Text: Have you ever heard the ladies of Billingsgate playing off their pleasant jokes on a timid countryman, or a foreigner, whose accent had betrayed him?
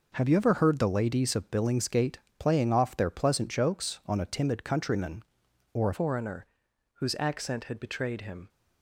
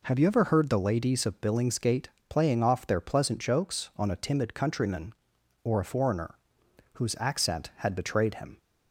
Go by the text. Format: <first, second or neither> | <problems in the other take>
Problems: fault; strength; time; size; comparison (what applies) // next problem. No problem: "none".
second | pauses between "Billingsgate" and "playing"; slight; at 2.1 s; 0.20 s long; slight in the second // changes voice at "foreigner"; from 5.9 s on; 2.5 s long